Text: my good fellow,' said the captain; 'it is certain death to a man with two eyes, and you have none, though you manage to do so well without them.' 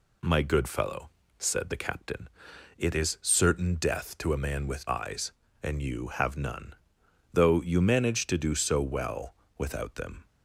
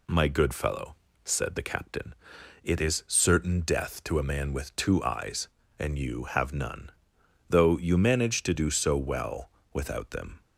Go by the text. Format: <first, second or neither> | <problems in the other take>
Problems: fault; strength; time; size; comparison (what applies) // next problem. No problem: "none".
second | skips "two"; at 4.8 s // pauses between "well" and "without"; slight; at 9.3 s; 0.22 s long; slight in the second